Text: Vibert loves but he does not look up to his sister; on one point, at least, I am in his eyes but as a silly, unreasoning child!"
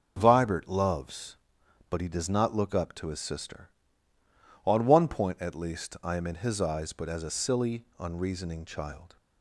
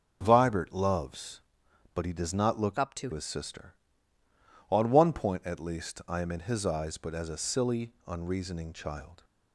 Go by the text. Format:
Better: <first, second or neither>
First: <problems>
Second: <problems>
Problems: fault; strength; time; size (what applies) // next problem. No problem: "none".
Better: first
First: starts louder than the rest; until 1.1 s; 6 dB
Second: starts louder than the rest; noticeable; until 1.2 s; 6 dB // changes voice from "up" to "to"; from 2.7 to 3.1 s; 0.4 s long